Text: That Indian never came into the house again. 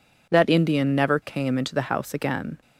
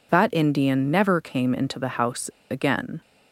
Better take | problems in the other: first | pauses between "house" and "again"; slight; at 2.2 s; 0.22 s long

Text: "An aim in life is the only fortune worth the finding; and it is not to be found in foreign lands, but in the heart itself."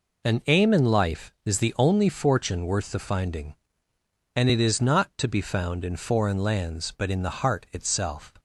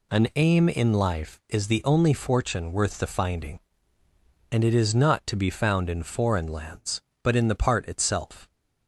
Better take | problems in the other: first | says "part" for "heart"; at 7.5 s

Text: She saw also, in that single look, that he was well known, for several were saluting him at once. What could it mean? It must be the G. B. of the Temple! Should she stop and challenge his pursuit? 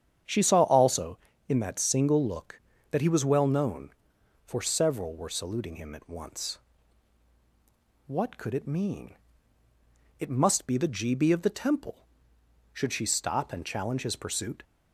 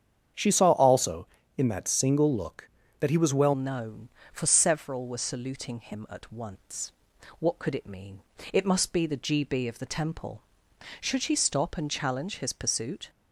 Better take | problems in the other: first | starts louder than the rest; strong; until 1.6 s; 8 dB; strong in the first // changes voice at "known"; from 3.5 s on; 9.5 s long

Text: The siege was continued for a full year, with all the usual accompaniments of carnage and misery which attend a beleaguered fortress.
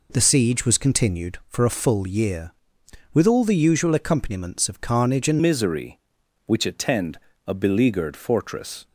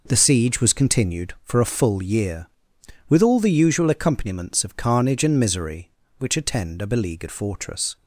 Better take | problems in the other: second | changes voice at "misery"; from 5.4 s on; 3.4 s long // pauses between "attend" and "a"; slight; at 7.1 s; 0.30 s long

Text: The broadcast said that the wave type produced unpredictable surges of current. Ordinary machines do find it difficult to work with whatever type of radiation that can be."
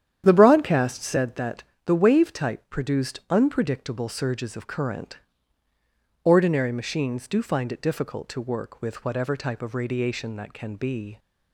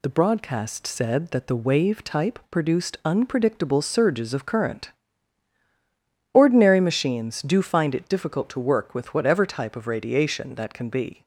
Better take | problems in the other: second | starts louder than the rest; strong; until 1.3 s; 9.5 dB // pauses between "that" and "the"; slight; at 1.6 s; 0.20 s long

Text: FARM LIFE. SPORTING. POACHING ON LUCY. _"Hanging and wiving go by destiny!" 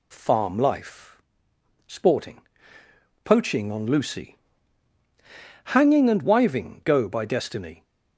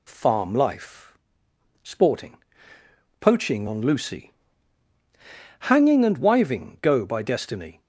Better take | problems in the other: neither | none

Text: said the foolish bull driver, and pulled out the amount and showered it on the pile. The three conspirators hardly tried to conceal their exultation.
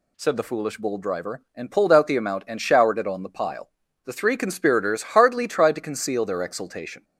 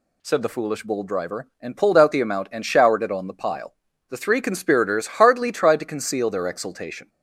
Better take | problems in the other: neither | none

